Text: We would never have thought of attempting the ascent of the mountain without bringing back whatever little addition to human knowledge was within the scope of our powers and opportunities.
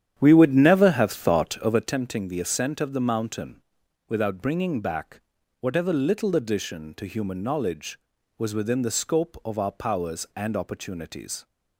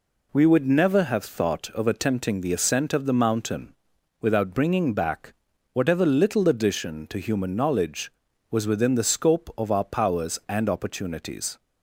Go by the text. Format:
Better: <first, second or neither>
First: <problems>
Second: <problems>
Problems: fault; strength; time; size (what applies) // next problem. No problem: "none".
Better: second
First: starts louder than the rest; strong; until 1.9 s; 10 dB // pauses between "mountain" and "without"; noticeable; at 3.6 s; 0.48 s long // pauses between "back" and "whatever"; at 5.2 s; 0.40 s long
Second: pauses between "mountain" and "without"; noticeable; at 3.7 s; 0.48 s long // pauses between "back" and "whatever"; at 5.3 s; 0.40 s long